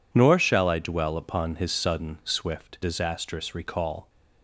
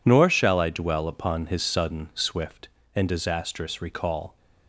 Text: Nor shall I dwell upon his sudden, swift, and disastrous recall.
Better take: second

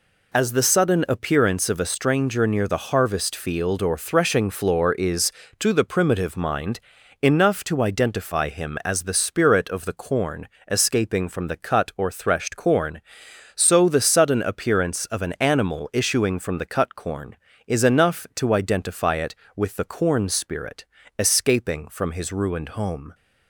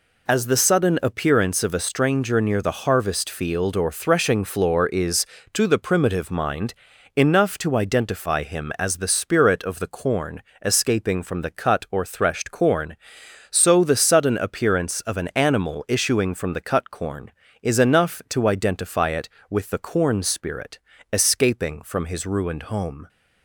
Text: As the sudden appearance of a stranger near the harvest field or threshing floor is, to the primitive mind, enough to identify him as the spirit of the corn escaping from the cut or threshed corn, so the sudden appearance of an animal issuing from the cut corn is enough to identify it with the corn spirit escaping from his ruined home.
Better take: neither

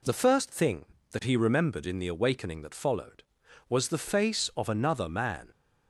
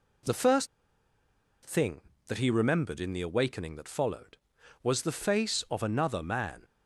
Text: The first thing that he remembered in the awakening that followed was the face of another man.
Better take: first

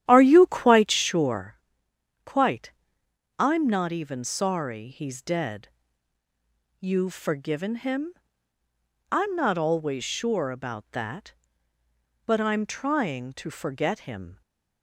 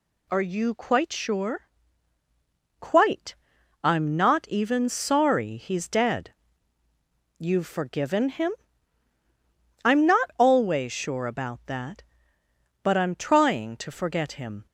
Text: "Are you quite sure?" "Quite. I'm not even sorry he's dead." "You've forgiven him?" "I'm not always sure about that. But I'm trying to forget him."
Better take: second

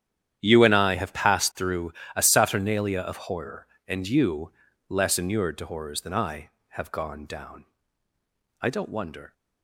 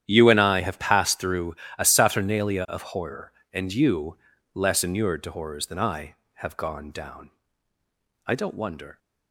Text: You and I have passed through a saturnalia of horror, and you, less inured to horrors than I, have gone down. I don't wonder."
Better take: neither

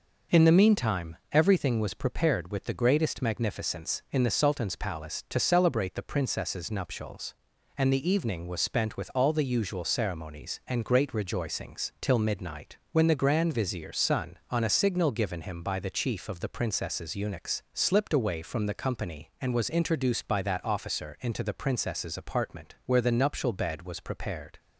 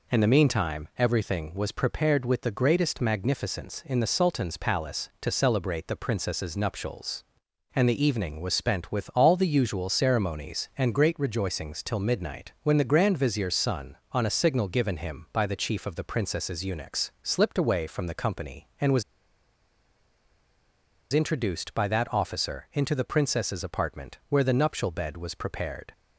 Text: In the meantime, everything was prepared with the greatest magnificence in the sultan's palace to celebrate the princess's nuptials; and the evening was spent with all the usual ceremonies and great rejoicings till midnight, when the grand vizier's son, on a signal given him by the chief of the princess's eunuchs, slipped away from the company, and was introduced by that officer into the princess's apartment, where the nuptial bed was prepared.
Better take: first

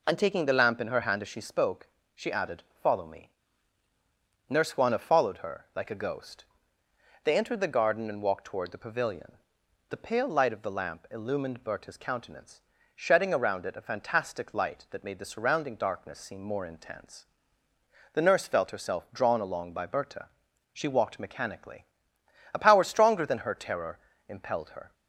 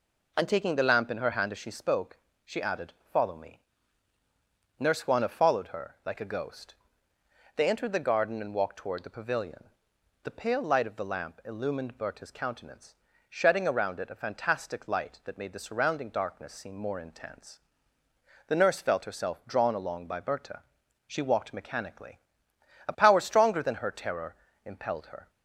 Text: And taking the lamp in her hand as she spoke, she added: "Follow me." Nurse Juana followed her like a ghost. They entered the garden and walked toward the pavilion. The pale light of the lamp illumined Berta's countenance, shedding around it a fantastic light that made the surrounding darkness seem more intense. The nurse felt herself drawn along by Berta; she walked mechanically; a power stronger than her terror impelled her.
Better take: neither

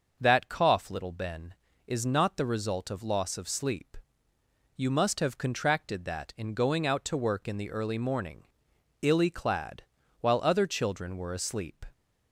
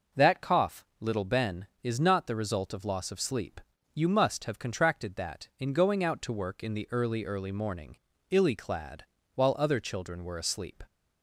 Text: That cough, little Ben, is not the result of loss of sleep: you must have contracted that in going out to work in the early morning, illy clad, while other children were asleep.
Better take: first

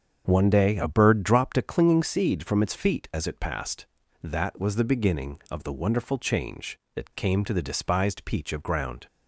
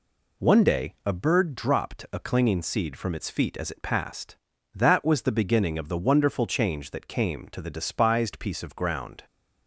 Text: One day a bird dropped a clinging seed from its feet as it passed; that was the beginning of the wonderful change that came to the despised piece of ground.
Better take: second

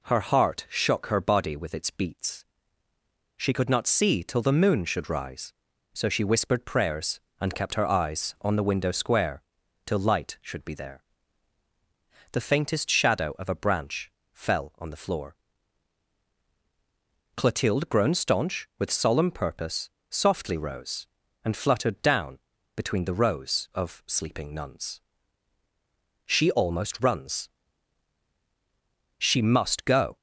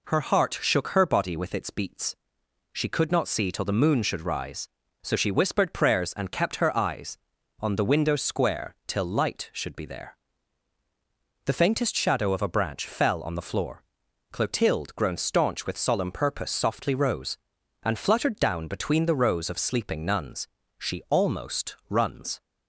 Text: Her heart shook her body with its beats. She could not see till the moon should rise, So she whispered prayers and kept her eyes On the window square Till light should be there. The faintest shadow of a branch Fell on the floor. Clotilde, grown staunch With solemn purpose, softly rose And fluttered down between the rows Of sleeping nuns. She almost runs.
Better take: second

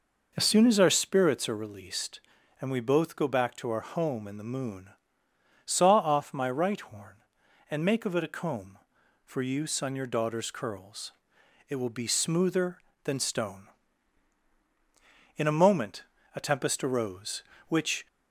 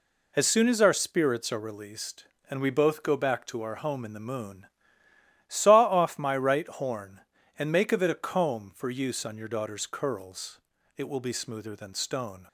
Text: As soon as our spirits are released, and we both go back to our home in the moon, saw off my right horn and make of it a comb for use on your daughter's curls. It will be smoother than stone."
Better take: second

